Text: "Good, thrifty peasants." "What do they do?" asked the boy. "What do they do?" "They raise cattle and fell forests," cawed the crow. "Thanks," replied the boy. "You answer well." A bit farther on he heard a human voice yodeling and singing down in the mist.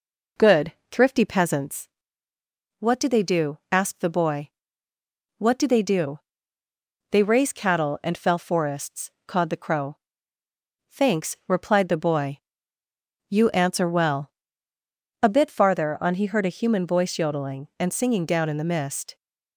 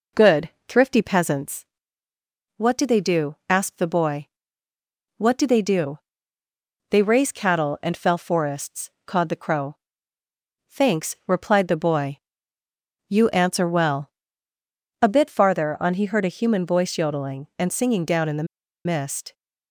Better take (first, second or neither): first